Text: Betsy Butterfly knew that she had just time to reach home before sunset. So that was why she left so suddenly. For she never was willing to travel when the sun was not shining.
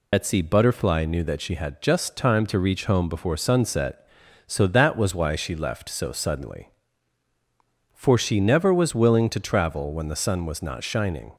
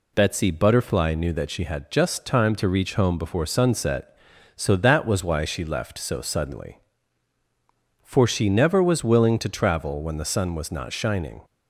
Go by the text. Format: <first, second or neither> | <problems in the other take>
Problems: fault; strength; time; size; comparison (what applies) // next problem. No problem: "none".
second | loses the start of "Betsy"; at 0.1 s; 75 ms